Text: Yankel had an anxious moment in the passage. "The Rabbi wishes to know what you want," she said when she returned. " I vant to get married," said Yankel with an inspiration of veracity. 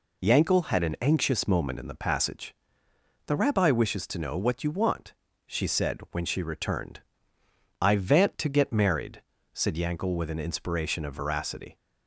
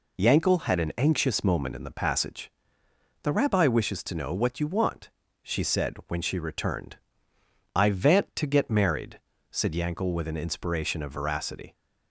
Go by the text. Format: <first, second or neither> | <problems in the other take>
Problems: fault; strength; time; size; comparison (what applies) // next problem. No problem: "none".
neither | none